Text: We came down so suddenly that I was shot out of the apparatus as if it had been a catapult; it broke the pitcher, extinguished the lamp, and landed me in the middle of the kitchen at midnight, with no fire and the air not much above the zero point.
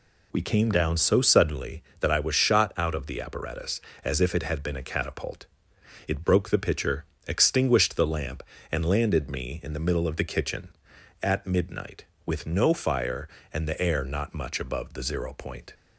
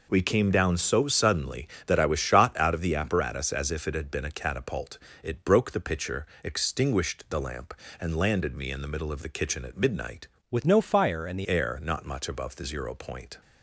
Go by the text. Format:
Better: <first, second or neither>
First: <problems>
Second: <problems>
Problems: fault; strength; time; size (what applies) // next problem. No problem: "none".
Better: first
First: none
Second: changes voice from "with" to "the"; from 10.5 to 11.4 s; 0.9 s long